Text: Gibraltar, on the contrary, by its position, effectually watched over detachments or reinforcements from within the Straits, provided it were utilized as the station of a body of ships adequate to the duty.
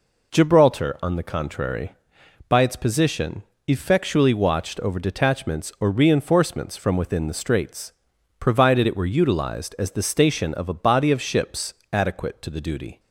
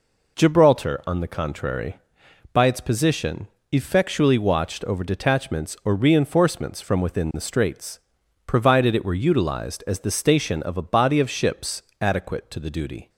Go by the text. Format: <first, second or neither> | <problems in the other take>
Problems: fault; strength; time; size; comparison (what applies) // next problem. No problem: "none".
neither | pauses between "ships" and "adequate"; slight; the same in both